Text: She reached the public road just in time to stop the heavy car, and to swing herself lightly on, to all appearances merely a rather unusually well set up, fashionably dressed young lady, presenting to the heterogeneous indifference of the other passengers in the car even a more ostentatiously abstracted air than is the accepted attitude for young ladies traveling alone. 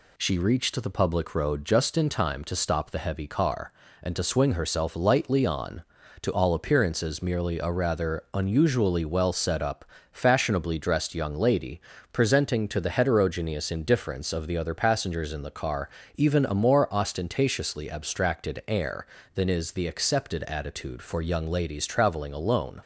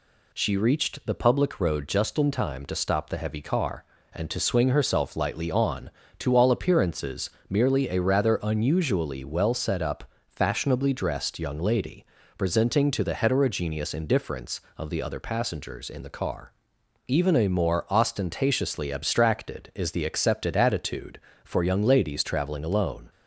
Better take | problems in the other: first | pauses between "appearances" and "merely"; slight; at 7.3 s; 0.20 s long // pauses between "car" and "even"; noticeable; at 16.5 s; 0.56 s long; slight in the first // skips "air than"; at 19.7 s

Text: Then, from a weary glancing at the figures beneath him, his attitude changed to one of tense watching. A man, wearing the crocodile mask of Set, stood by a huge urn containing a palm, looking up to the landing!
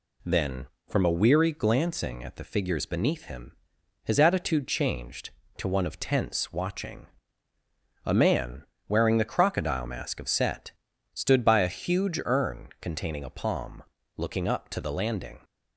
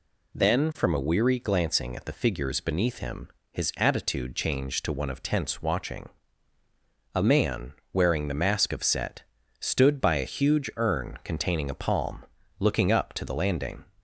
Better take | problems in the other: first | skips "crocodile"; at 8.3 s

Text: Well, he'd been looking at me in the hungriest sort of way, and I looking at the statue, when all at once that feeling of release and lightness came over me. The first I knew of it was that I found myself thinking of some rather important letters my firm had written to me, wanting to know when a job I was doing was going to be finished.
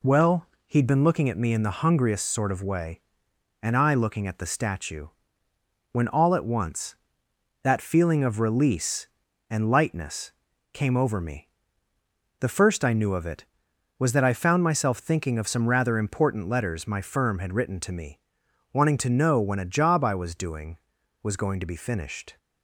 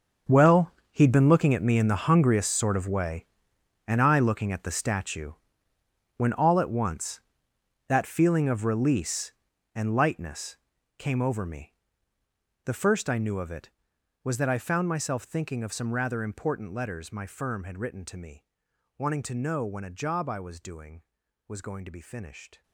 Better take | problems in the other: first | gets quieter; strong; throughout; 15.5 dB // pauses between "lightness" and "came"; at 10.5 s; 0.42 s long; also in the first

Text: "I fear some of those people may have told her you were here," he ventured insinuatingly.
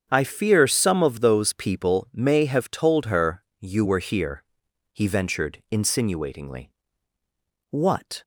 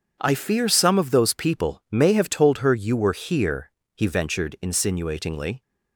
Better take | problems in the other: second | starts louder than the rest; strong; until 1.1 s; 7.5 dB // pauses between "her" and "you"; slight; at 3.4 s; 0.16 s long // goes on to say "What"; from 7.7 s on; 0.52 s long

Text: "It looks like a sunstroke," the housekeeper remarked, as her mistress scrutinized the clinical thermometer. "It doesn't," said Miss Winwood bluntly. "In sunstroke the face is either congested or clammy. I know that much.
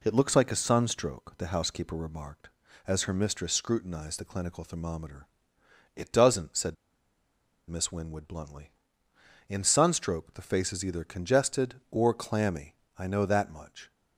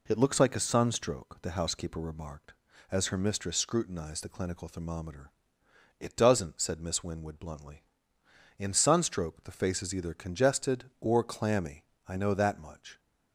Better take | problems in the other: second | pauses between "said" and "Miss"; noticeable; at 6.7 s; 0.93 s long

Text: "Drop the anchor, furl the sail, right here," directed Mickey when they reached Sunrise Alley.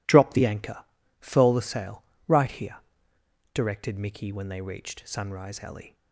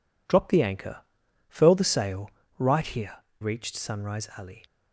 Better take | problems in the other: first | skips "directed Mickey when they"; at 3.2 s

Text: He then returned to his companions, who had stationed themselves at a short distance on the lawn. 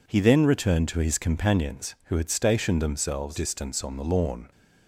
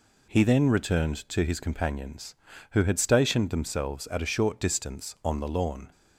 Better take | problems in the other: second | skips "at a short"; at 3.3 s

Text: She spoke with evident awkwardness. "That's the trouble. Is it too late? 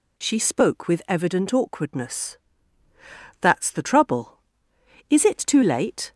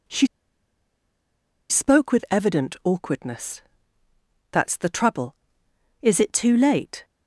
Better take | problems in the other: first | pauses between "She" and "spoke"; strong; at 0.2 s; 1.4 s long

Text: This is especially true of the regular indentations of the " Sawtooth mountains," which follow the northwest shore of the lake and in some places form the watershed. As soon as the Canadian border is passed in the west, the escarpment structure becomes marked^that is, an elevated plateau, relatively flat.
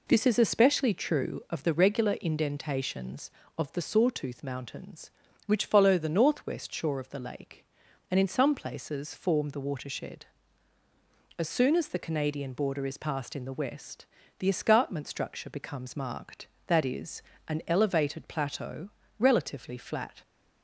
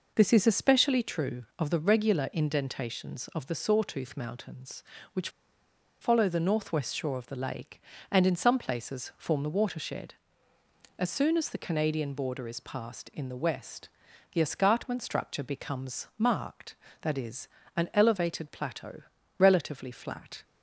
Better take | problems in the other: first | pauses between "which" and "follow"; noticeable; at 5.2 s; 0.72 s long

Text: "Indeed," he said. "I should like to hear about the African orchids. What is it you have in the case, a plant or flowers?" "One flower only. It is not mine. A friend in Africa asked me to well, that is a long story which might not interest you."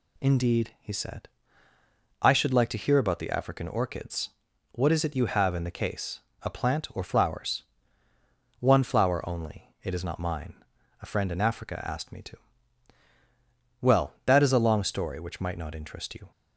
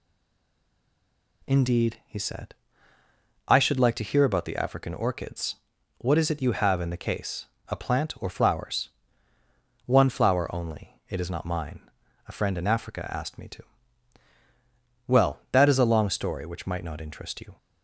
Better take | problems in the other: first | stays silent before the first word; noticeable; until 1.4 s; 1.4 s long // pauses between "to" and "well"; strong; at 13.6 s; 1.4 s long; strong in the first

